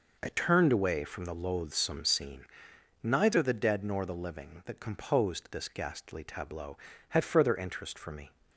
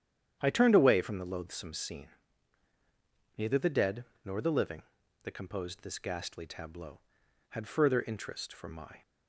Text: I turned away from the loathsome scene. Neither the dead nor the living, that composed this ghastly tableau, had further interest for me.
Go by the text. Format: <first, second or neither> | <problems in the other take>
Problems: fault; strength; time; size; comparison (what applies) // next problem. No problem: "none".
first | starts louder than the rest; strong; until 1.4 s; 9.5 dB // pauses between "dead" and "nor"; slight; at 4.0 s; 0.20 s long // says "my" for "me"; at 8.6 s